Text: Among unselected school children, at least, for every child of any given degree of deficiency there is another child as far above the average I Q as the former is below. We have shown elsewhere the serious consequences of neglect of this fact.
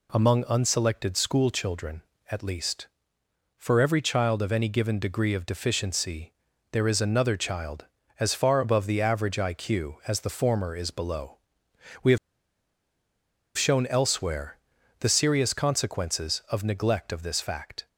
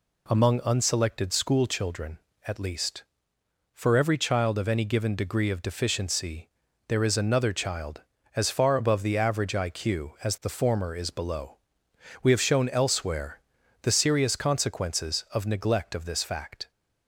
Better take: second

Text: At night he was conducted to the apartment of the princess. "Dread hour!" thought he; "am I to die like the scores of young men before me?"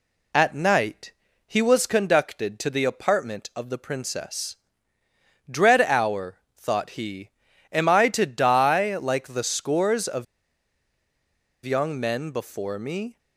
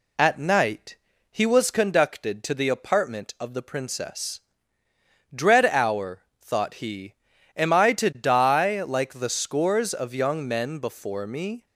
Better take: second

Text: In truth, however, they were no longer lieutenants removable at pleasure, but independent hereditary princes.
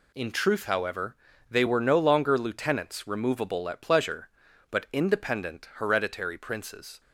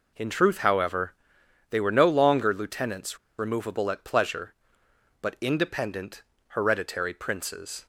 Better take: first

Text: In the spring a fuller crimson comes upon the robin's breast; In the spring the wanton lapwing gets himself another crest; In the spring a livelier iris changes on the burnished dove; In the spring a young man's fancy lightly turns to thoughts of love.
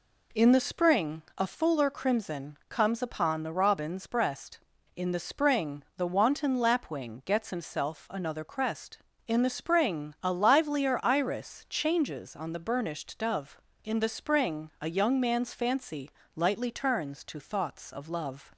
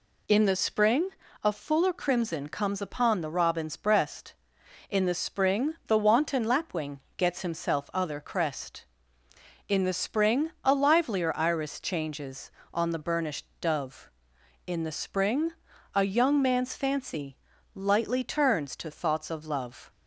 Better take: first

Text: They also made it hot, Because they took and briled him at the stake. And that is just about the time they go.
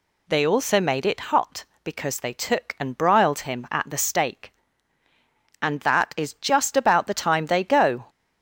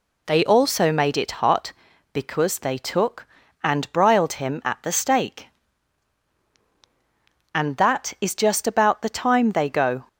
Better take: neither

